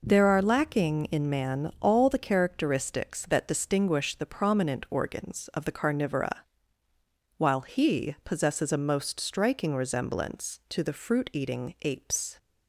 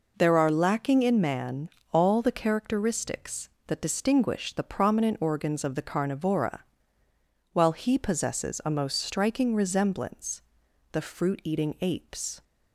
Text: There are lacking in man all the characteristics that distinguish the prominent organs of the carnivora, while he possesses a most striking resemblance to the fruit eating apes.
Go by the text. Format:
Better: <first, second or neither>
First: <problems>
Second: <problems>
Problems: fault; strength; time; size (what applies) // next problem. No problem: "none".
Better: first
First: none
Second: pauses between "man" and "all"; slight; at 1.6 s; 0.22 s long // skips "to"; at 10.6 s